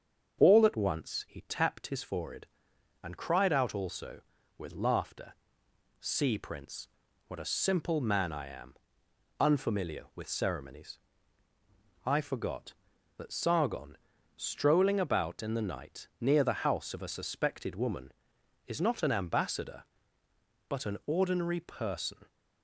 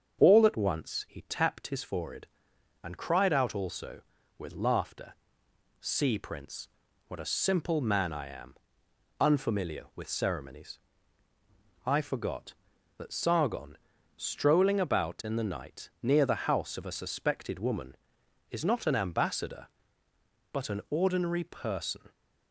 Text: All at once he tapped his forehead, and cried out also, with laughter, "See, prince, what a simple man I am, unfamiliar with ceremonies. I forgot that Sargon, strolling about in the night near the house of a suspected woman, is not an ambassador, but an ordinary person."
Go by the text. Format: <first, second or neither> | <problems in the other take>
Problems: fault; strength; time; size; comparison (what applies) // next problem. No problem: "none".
neither | starts louder than the rest; the same in both